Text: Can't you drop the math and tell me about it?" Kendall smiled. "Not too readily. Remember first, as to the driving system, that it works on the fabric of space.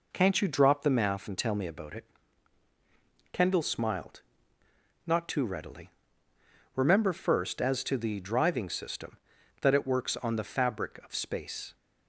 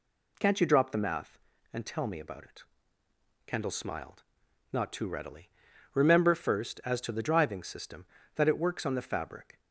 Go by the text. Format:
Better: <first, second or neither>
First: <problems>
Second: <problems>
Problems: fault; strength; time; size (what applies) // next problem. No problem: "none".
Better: first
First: none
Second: stops before "of space"; at 9.5 s